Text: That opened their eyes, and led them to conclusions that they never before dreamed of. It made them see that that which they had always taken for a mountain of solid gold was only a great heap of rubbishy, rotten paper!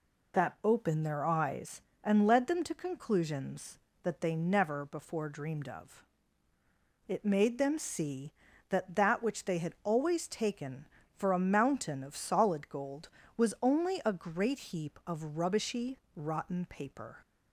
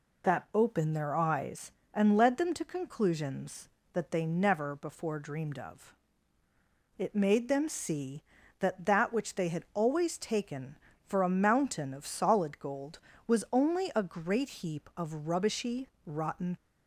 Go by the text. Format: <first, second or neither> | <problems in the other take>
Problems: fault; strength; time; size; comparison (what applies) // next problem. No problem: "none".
first | stops before "paper"; at 16.5 s